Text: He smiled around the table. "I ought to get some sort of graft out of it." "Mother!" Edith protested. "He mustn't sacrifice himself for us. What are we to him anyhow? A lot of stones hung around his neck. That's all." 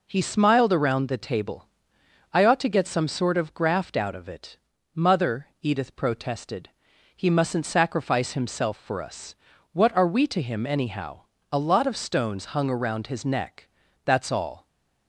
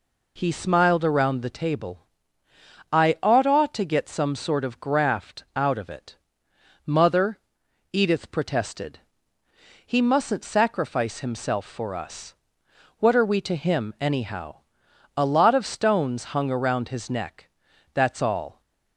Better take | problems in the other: first | says "ought" twice; at 3.4 s

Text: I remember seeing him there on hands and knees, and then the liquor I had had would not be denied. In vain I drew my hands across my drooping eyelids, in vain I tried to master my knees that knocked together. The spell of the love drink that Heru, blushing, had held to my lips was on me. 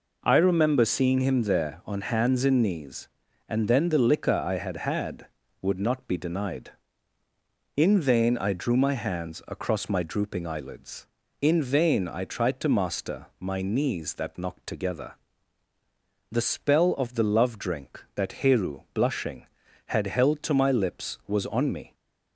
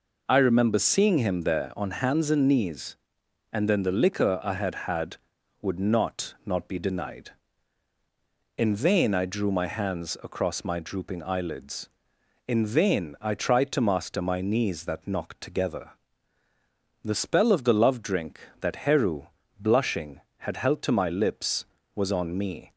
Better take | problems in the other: first | says "not" twice; at 6.4 s

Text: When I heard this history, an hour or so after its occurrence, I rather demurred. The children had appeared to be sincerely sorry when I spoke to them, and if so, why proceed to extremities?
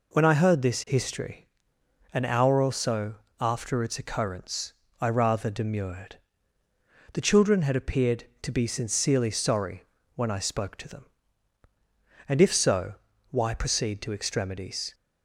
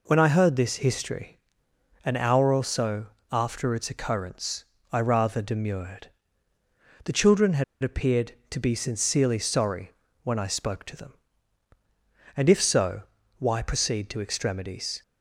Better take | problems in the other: first | pauses between "so" and "after"; slight; at 3.0 s; 0.24 s long; slight in the first // pauses between "had" and "appeared"; slight; at 7.6 s; 0.19 s long // pauses between "sorry" and "when"; slight; at 9.8 s; 0.32 s long; slight in the first

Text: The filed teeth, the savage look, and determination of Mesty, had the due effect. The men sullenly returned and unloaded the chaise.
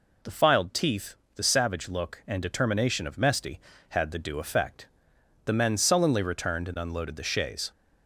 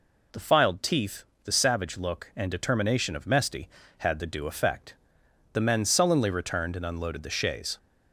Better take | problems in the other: neither | none

